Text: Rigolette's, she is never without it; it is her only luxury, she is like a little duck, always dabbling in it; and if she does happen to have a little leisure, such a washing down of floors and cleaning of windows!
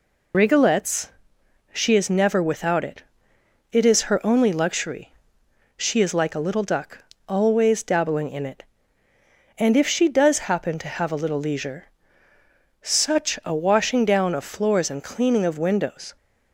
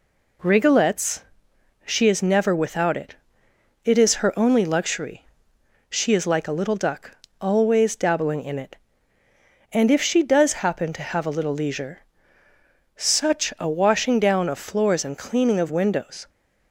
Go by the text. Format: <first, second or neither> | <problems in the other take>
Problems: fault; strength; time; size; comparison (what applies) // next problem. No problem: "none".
second | loses the start of "Rigolette's"; at 0.3 s; 70 ms